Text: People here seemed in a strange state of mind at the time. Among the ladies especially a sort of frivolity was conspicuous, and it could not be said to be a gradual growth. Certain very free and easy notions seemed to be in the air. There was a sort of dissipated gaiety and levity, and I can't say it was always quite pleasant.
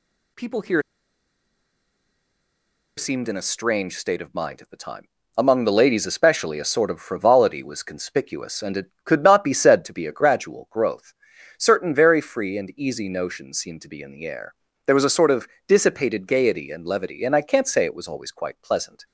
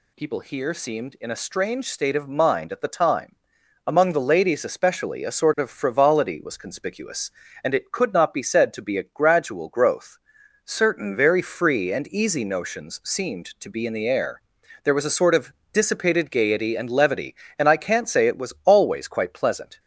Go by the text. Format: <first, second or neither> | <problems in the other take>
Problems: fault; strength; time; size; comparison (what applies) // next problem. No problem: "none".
second | pauses between "here" and "seemed"; strong; at 0.8 s; 2.1 s long // pauses between "of" and "dissipated"; slight; at 15.4 s; 0.20 s long; slight in the second